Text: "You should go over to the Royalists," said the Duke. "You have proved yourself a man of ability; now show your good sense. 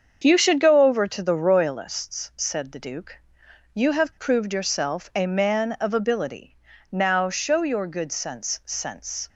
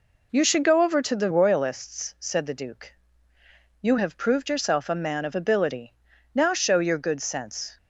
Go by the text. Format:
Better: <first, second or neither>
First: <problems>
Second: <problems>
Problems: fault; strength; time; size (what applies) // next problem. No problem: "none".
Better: second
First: starts louder than the rest; until 1.2 s; 7 dB // says "sense" twice; at 8.6 s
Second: none